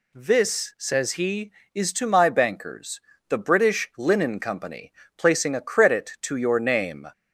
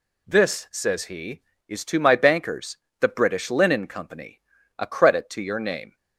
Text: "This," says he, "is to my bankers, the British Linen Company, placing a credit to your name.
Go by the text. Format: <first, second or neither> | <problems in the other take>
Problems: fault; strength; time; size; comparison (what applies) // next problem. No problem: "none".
first | skips "placing"; at 4.5 s